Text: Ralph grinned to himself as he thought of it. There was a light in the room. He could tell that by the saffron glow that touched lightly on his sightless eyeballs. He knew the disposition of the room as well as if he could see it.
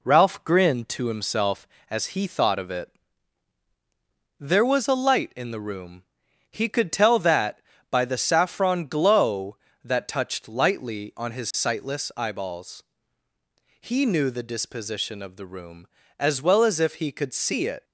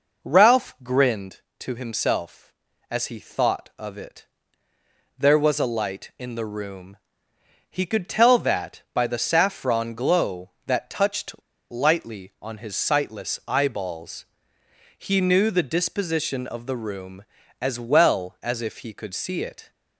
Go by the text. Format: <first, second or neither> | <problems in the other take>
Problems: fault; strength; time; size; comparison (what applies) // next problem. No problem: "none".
first | pauses between "touched" and "lightly"; at 11.3 s; 0.36 s long